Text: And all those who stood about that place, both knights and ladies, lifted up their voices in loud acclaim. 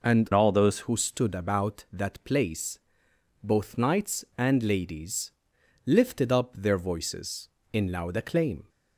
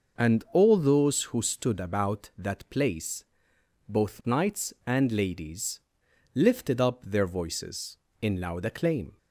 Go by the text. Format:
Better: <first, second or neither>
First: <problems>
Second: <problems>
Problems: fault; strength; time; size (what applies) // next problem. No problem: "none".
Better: second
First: changes voice from "all" to "those"; from 0.3 to 0.7 s; 0.4 s long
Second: none